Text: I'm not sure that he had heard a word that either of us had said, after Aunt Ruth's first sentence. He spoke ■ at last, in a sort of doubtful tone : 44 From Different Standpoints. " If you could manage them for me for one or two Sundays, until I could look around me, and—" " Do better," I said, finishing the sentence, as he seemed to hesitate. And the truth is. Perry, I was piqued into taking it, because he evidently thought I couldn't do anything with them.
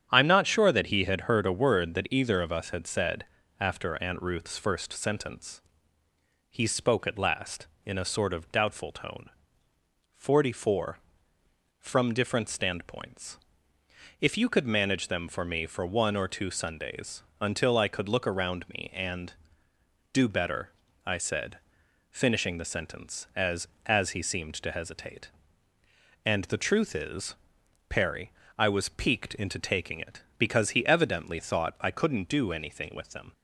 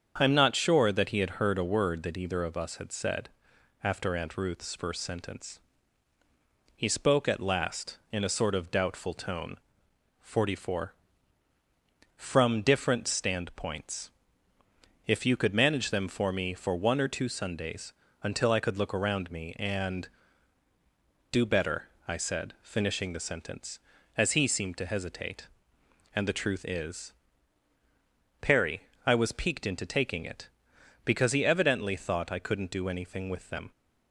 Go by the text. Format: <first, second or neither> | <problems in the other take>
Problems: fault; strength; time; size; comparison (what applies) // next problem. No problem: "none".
second | starts louder than the rest; strong; until 1.1 s; 8.5 dB; strong in the second // says "as" twice; at 23.8 s